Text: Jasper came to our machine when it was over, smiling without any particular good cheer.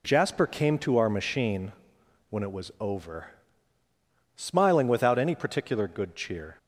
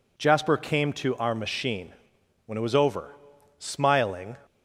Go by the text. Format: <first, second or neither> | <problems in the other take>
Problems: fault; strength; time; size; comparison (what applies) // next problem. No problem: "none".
first | pauses between "machine" and "when"; noticeable; at 1.9 s; 0.54 s long; noticeable in the first // stops before "without any particular good cheer"; at 4.4 s